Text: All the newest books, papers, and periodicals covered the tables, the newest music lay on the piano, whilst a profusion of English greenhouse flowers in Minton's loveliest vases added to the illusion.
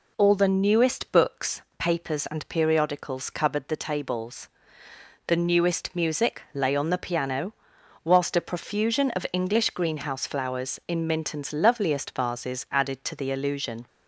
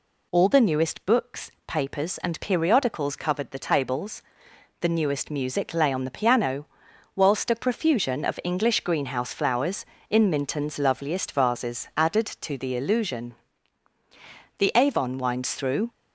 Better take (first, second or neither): first